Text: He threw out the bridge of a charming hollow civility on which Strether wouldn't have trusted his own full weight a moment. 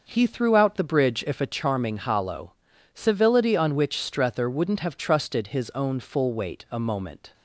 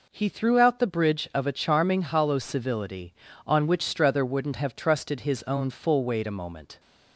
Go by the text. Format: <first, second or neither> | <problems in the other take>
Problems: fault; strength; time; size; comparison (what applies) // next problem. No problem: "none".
second | says "if" for "of"; at 1.2 s // pauses between "hollow" and "civility"; at 2.5 s; 0.42 s long